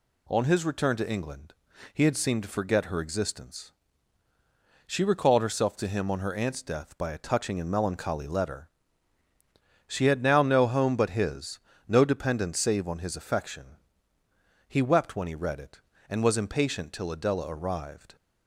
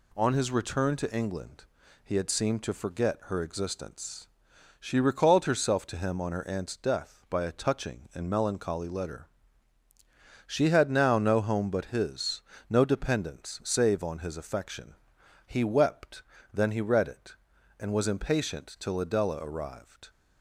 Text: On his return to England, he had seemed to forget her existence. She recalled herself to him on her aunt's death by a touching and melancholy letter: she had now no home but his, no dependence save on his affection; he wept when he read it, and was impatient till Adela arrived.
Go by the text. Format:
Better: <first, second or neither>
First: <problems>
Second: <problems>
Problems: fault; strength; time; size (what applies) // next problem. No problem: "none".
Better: first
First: none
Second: says "then" for "when"; at 16.5 s